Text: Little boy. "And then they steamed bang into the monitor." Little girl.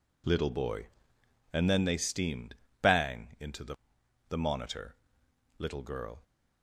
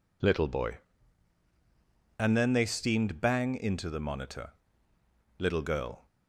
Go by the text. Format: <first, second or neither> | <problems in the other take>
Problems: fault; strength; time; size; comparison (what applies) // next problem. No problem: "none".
second | pauses between "steamed" and "bang"; slight; at 2.5 s; 0.26 s long // says "the" twice; at 4.2 s